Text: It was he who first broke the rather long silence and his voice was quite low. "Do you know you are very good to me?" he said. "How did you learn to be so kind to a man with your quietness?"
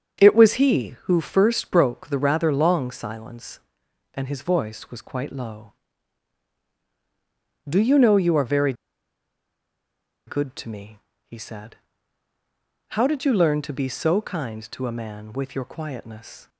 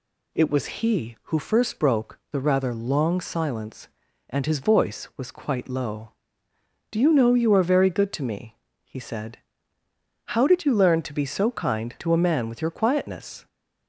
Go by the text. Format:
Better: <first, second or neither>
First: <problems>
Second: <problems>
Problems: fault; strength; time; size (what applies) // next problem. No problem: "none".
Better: second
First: starts louder than the rest; until 1.2 s; 7 dB // pauses between "very" and "good"; strong; at 8.7 s; 1.5 s long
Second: none